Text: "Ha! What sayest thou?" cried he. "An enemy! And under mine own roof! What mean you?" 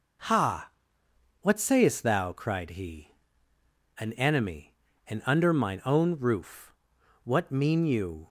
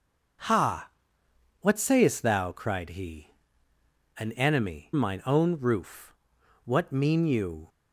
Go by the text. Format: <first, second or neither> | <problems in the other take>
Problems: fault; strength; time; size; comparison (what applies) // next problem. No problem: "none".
first | skips "And under"; at 4.9 s